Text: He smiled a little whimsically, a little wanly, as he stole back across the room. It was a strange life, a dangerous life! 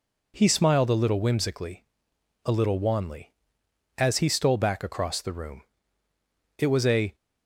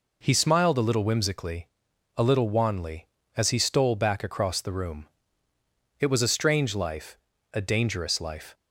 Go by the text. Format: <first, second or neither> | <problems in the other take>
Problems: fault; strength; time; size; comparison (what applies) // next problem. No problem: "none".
second | stops before "strange life a dangerous life"; at 7.1 s